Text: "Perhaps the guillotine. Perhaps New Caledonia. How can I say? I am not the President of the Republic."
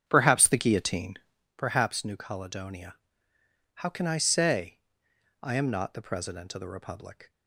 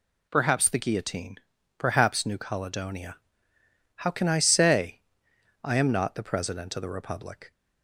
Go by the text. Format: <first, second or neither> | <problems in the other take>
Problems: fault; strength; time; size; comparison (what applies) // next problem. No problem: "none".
second | starts louder than the rest; strong; until 1.5 s; 8.5 dB